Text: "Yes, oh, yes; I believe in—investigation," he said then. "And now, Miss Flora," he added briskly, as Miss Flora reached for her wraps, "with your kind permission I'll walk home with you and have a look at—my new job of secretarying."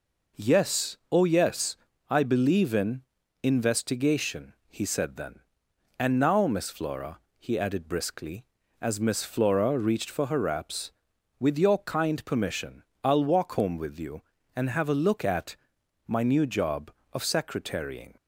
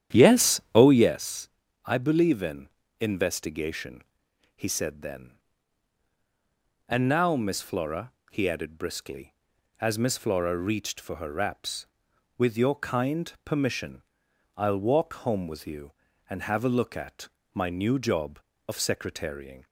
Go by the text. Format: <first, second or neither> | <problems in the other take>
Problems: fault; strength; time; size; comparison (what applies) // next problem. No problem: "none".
first | starts louder than the rest; strong; until 1.2 s; 10 dB // pauses between "permission" and "I'll"; noticeable; at 14.0 s; 0.56 s long; slight in the first